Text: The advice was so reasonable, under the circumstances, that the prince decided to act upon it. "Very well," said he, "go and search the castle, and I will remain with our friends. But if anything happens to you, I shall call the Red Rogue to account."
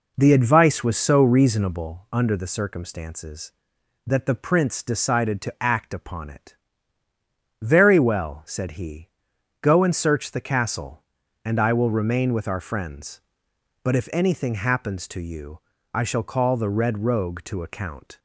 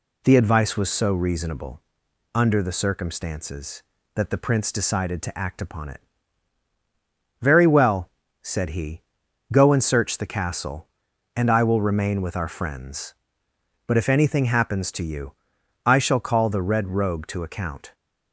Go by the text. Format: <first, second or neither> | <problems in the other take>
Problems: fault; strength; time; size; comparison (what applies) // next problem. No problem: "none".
second | starts louder than the rest; noticeable; until 2.0 s; 4.5 dB